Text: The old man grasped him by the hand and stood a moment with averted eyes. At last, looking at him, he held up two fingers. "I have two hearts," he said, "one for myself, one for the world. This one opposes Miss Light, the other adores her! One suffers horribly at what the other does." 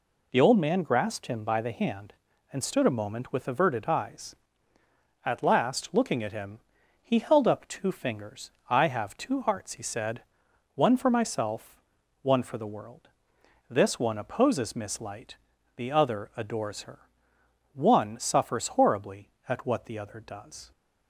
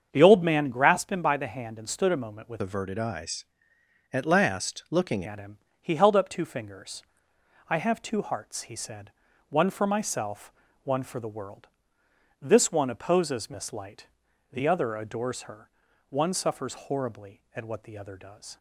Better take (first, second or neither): first